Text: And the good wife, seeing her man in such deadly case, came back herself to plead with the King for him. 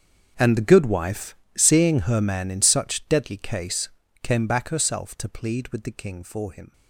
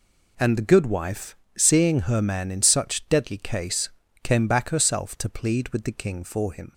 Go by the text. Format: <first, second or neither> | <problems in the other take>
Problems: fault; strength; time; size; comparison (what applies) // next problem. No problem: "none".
second | gets quieter; strong; throughout; 18.5 dB